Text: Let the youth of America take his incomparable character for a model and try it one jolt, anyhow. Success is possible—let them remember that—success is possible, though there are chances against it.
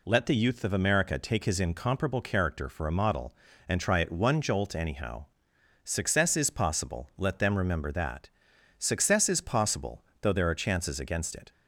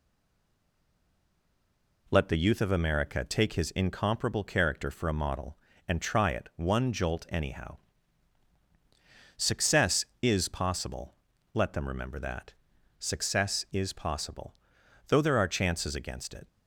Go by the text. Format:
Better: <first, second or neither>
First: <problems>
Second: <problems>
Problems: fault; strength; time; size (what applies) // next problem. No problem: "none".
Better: first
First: none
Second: stays silent before the first word; noticeable; until 2.0 s; 2.0 s long